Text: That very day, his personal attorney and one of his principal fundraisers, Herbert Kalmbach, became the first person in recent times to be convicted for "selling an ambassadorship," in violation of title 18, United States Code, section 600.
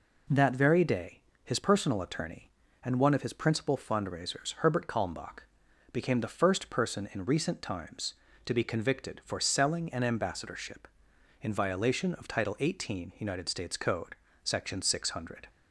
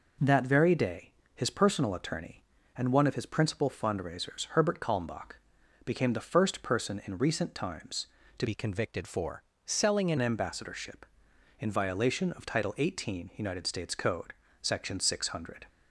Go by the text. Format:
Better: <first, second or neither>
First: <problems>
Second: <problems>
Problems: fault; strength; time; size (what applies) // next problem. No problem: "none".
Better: first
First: none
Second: changes voice from "be" to "an"; from 8.4 to 10.1 s; 1.7 s long // pauses between "for" and "selling"; slight; at 9.4 s; 0.24 s long